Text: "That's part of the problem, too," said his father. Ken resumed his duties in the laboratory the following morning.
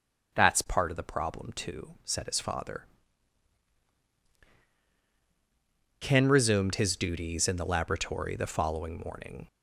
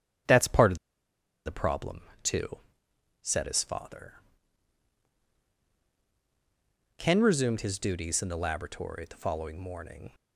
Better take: first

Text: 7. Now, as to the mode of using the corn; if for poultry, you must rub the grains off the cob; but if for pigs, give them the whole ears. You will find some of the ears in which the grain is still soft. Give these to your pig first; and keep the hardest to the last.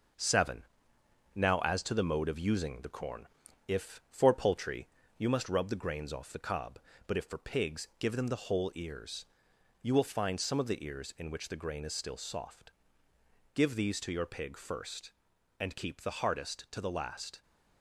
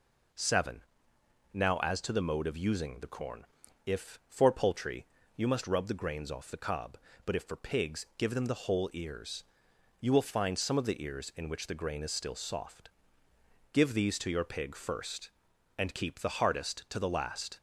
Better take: second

